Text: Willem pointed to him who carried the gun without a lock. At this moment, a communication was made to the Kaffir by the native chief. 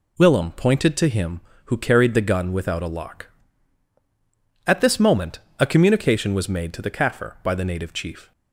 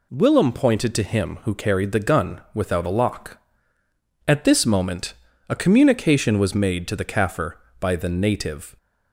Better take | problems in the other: first | stops before "chief"; at 8.7 s

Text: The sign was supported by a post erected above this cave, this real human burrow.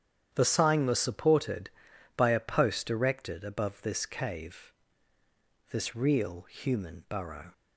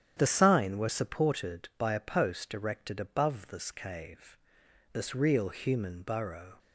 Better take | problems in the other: first | starts louder than the rest; strong; until 1.1 s; 9.5 dB; strong in the first // says "were" for "was"; at 0.7 s

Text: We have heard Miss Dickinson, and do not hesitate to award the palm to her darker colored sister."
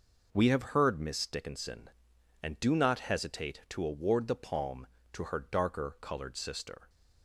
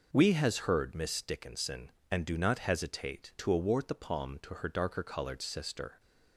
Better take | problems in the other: first | says "has" for "have"; at 0.3 s

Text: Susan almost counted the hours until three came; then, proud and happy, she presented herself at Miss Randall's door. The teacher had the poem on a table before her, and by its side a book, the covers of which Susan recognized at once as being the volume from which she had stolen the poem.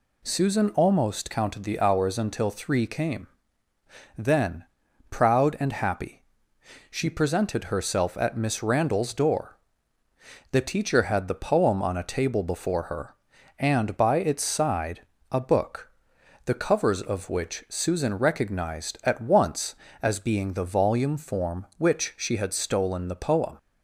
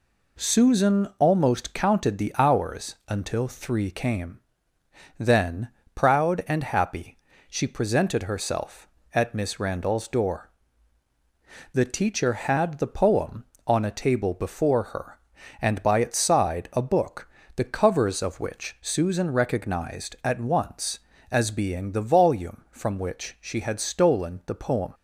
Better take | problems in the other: second | pauses between "side" and "a"; slight; at 15.0 s; 0.28 s long // says "form" for "from"; at 21.1 s

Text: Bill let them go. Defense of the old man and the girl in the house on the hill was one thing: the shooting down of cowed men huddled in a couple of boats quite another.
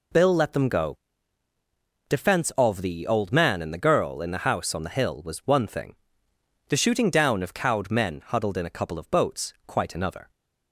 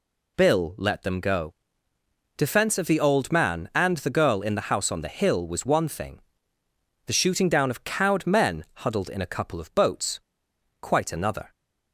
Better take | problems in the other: first | pauses between "men" and "huddled"; slight; at 8.6 s; 0.18 s long // pauses between "boats" and "quite"; noticeable; at 10.1 s; 0.61 s long

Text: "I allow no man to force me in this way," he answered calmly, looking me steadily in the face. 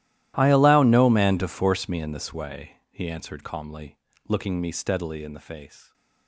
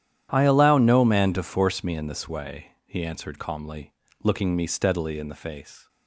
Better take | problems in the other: second | gets quieter; strong; throughout; 23.5 dB // starts louder than the rest; strong; until 1.3 s; 14 dB; strong in the second

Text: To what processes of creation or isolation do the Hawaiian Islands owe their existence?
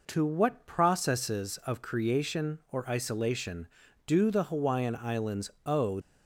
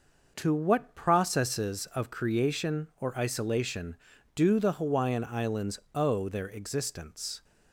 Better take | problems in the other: second | pauses between "Islands" and "owe"; slight; at 5.4 s; 0.16 s long; slight in the second // stops before "their existence"; at 6.0 s

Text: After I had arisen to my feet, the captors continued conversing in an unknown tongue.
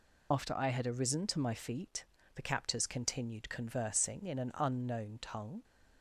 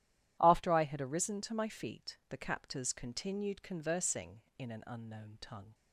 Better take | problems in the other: second | loses the start of "After"; at 0.3 s; 60 ms

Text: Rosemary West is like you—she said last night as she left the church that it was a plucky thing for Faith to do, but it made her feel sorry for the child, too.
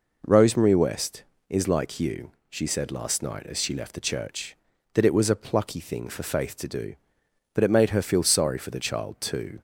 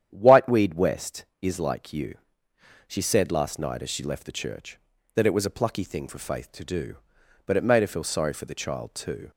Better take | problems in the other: first | starts louder than the rest; strong; until 1.1 s; 9.5 dB // says "Whiteweed" for "Rosemary"; at 0.1 s

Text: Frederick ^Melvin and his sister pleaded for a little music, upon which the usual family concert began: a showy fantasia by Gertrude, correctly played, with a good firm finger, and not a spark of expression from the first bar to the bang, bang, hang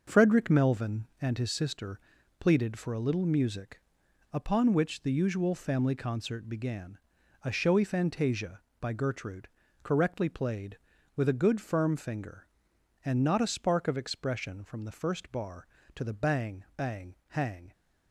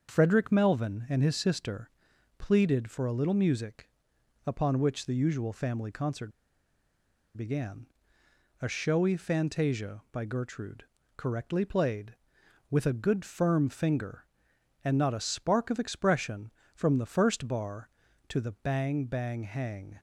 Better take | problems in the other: first | starts louder than the rest; until 1.1 s; 6.5 dB // pauses between "sister" and "pleaded"; noticeable; at 1.8 s; 0.52 s long; also in the first // pauses between "concert" and "began"; at 6.3 s; 1.0 s long

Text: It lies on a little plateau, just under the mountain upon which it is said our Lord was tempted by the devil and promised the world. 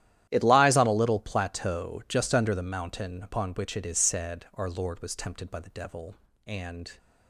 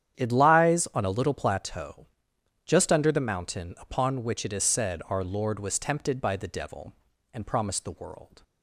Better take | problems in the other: second | starts louder than the rest; strong; until 1.3 s; 12 dB; strong in the second // stops before "promised the world"; at 6.9 s

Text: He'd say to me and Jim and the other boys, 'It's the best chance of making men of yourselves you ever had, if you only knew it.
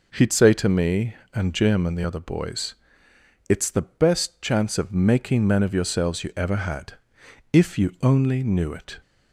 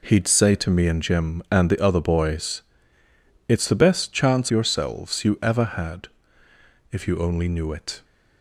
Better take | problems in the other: first | skips "of making men of"; at 4.4 s

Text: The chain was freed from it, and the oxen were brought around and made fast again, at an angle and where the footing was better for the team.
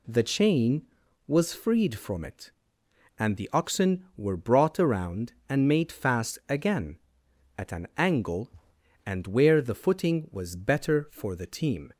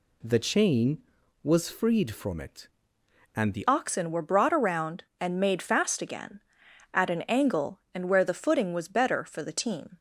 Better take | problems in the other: first | changes voice at "oxen"; from 3.6 s on; 6.3 s long

